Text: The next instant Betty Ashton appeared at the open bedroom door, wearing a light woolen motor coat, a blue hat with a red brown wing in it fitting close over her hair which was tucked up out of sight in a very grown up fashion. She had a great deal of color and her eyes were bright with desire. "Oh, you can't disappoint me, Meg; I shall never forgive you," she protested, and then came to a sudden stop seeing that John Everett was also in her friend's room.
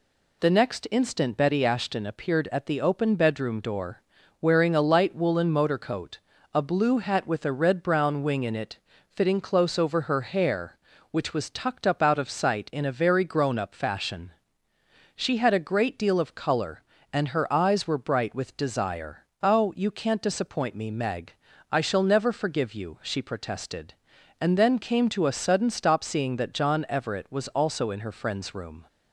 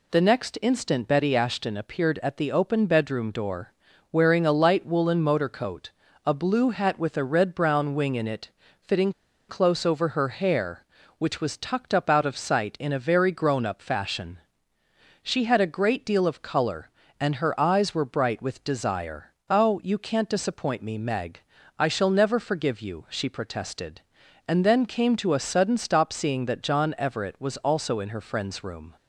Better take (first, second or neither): first